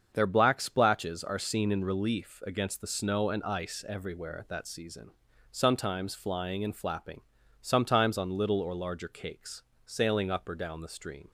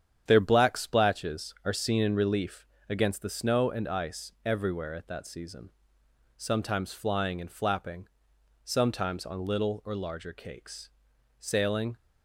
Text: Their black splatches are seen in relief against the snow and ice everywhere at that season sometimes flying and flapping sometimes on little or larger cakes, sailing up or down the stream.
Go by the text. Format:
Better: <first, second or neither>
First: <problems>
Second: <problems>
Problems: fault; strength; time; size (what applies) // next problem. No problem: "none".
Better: first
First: starts louder than the rest; until 1.1 s; 7 dB // pauses between "season" and "sometimes"; at 5.1 s; 0.42 s long // pauses between "flapping" and "sometimes"; at 7.2 s; 0.40 s long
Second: starts louder than the rest; strong; until 1.2 s; 9 dB // pauses between "relief" and "against"; slight; at 2.6 s; 0.24 s long // pauses between "season" and "sometimes"; noticeable; at 5.6 s; 0.68 s long // pauses between "flapping" and "sometimes"; noticeable; at 8.0 s; 0.56 s long // stops before "up or down the stream"; at 11.9 s